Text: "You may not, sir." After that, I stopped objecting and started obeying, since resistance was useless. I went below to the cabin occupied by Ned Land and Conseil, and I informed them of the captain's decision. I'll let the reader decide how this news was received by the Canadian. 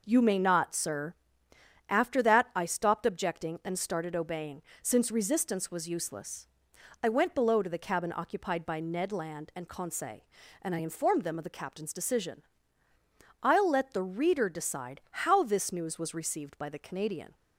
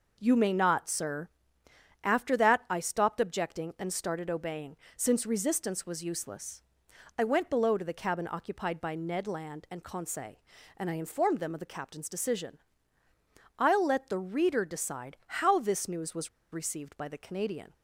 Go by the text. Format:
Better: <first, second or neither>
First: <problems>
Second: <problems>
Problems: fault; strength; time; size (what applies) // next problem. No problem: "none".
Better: first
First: none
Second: pauses between "was" and "received"; slight; at 16.2 s; 0.24 s long